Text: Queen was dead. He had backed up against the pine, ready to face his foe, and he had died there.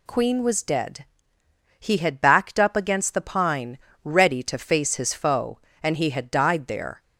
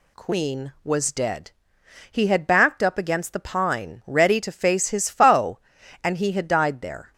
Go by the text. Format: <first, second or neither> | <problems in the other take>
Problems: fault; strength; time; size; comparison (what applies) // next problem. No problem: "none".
neither | none